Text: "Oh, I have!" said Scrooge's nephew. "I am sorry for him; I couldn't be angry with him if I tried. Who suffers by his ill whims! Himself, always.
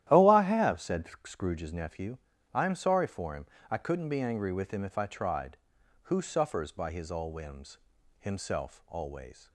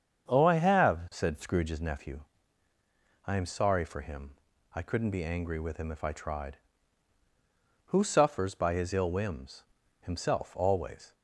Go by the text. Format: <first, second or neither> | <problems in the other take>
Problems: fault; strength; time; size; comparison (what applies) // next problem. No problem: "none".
second | starts louder than the rest; strong; until 1.3 s; 12.5 dB; strong in the second // pauses between "said" and "Scrooge's"; slight; at 1.0 s; 0.20 s long // says "all" for "ill"; at 7.1 s